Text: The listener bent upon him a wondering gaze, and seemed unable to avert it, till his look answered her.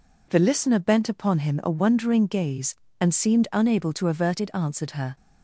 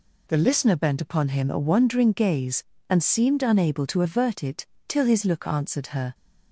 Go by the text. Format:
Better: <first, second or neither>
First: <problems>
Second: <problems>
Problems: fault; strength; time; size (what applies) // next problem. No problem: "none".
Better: second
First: skips "till his look"; at 4.5 s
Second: none